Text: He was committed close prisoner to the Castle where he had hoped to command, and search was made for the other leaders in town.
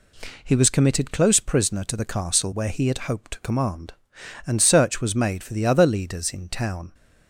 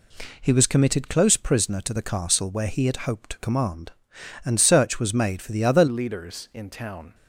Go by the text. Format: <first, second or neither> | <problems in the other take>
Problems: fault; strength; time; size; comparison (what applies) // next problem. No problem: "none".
first | changes voice at "leaders"; from 5.8 s on; 1.3 s long